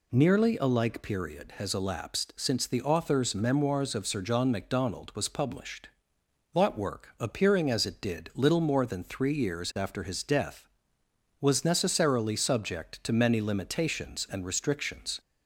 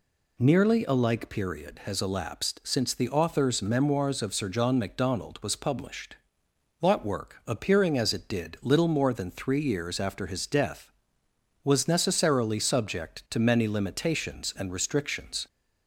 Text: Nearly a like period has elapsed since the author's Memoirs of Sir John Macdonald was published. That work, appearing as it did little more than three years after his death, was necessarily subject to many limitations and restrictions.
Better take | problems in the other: neither | none

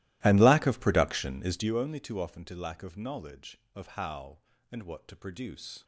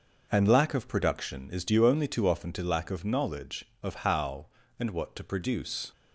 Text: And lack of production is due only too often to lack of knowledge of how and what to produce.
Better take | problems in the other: second | starts louder than the rest; strong; until 1.7 s; 17 dB

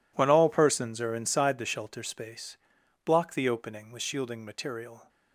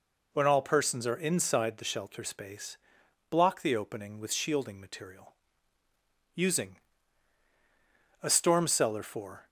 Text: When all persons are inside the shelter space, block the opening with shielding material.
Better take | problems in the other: first | goes on to say "USING A STORM CELLAR FOR"; strong; from 6.3 s on; 3.1 s long

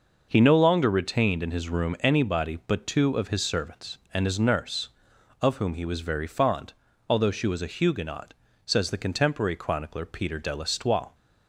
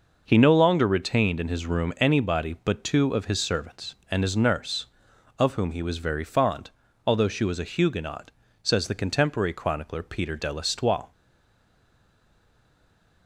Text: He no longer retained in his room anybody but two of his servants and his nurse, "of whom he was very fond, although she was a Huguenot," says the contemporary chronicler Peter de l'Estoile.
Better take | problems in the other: first | stays silent after the last word; from 11.1 s on; 2.1 s long

